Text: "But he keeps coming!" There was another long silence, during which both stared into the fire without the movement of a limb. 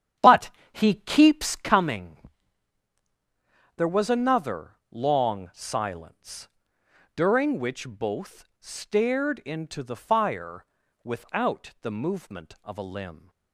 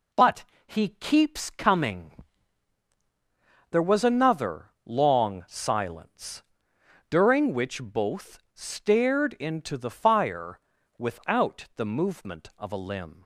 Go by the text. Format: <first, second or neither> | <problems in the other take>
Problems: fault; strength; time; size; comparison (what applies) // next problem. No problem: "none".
second | starts louder than the rest; strong; until 1.8 s; 9.5 dB // pauses between "But" and "he"; slight; at 0.4 s; 0.22 s long; slight in the second // pauses between "fire" and "without"; at 10.6 s; 0.38 s long; also in the second